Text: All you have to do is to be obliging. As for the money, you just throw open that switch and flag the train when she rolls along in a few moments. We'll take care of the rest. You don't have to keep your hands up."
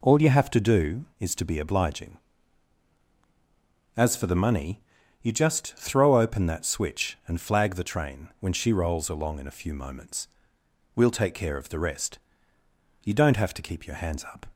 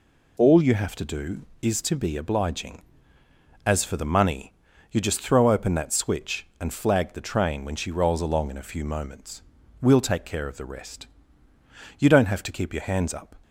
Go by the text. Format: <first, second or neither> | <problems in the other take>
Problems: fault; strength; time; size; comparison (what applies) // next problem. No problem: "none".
neither | none